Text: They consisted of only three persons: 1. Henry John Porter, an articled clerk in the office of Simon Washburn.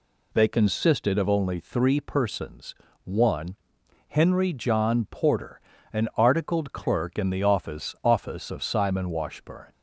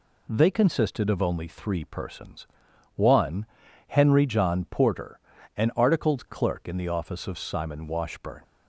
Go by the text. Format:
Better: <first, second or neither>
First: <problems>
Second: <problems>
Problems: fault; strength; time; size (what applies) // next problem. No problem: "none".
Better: second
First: says "office" twice; at 8.0 s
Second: none